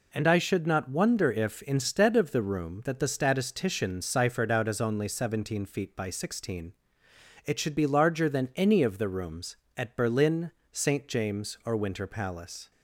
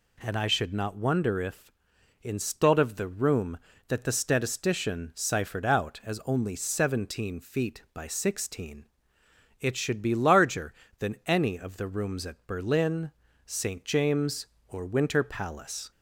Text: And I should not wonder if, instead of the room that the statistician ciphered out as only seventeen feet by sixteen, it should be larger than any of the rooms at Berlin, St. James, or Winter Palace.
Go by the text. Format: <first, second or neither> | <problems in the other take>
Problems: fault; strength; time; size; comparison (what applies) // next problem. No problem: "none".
neither | none